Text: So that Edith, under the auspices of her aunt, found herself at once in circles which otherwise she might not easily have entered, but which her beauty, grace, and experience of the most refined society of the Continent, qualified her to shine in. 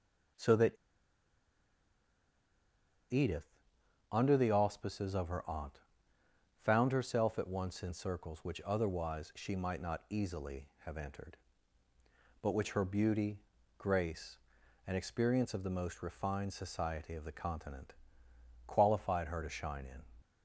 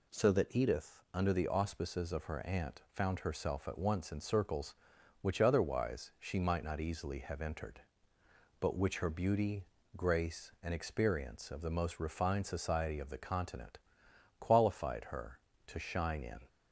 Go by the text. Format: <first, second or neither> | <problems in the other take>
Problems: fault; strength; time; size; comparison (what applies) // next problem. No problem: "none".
second | pauses between "that" and "Edith"; strong; at 0.7 s; 2.3 s long